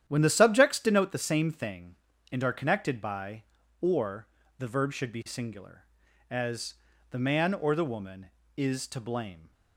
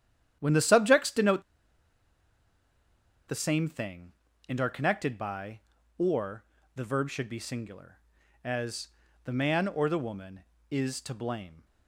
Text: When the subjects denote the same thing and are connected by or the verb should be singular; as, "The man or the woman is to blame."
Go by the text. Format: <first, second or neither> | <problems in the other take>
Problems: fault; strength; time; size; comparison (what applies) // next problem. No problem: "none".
first | starts louder than the rest; strong; until 1.4 s; 10 dB; strong in the first // pauses between "denote" and "the"; strong; at 1.4 s; 1.8 s long // pauses between "or" and "the"; slight; at 6.4 s; 0.32 s long; slight in the first